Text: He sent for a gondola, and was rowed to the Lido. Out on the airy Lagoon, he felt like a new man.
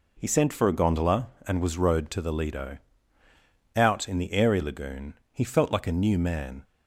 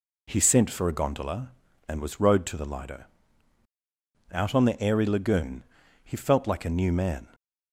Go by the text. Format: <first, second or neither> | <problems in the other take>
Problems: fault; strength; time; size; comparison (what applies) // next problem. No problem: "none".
second | says "in" for "on"; at 4.0 s